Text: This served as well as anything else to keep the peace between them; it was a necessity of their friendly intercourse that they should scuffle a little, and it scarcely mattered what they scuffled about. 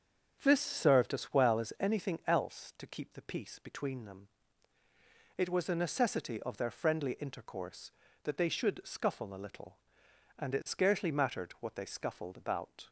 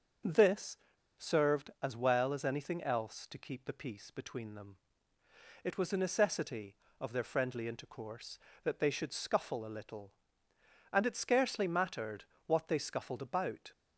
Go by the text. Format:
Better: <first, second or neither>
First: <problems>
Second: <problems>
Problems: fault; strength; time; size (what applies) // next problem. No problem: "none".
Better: first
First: starts louder than the rest; strong; until 1.4 s; 7.5 dB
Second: starts louder than the rest; until 1.6 s; 6.5 dB // pauses between "This" and "served"; at 0.7 s; 0.39 s long // pauses between "mattered" and "what"; slight; at 12.2 s; 0.20 s long